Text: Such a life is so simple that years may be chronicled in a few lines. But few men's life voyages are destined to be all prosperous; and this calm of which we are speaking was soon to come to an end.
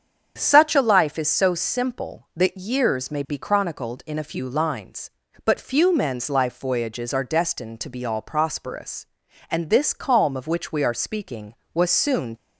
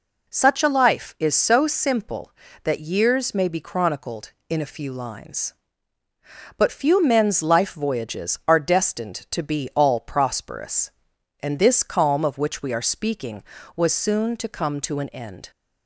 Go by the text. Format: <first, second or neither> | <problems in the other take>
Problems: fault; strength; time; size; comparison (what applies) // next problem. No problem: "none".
second | starts louder than the rest; strong; until 1.3 s; 7.5 dB // stops before "to come to an end"; at 12.3 s